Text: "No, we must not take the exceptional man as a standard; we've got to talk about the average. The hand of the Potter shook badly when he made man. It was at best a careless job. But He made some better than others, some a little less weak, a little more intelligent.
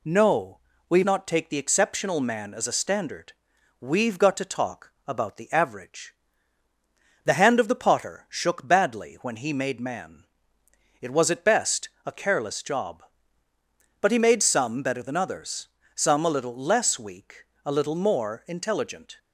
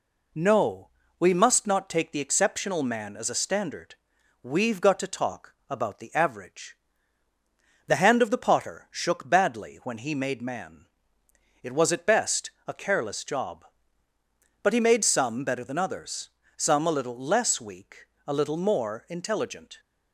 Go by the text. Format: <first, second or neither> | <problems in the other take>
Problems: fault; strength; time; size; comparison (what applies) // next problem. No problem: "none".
second | skips "must"; at 1.0 s // pauses between "best" and "a"; slight; at 11.8 s; 0.16 s long; slight in the second